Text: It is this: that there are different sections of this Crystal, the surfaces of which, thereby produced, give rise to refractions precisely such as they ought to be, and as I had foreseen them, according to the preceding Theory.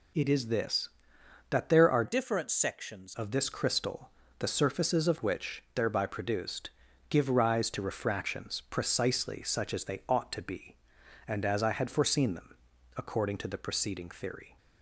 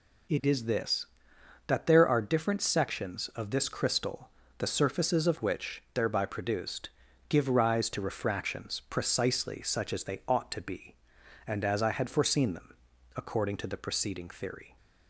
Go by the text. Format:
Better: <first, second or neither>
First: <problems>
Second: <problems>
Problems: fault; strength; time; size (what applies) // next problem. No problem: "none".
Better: second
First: changes voice from "different" to "sections"; from 2.0 to 3.1 s; 1.1 s long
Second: none